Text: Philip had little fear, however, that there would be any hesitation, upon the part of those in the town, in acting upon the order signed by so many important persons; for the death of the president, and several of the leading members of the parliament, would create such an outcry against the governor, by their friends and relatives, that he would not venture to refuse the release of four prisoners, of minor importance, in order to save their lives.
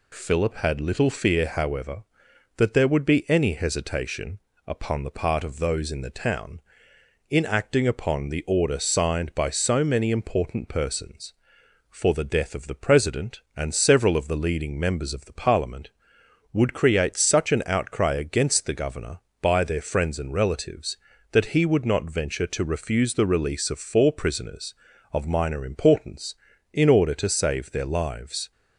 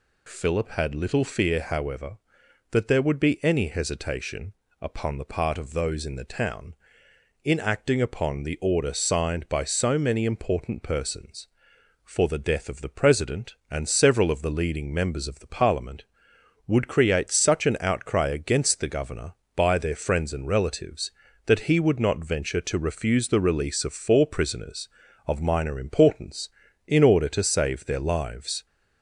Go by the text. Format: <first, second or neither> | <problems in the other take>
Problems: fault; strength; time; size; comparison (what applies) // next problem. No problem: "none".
first | gets louder; slight; throughout; 2.5 dB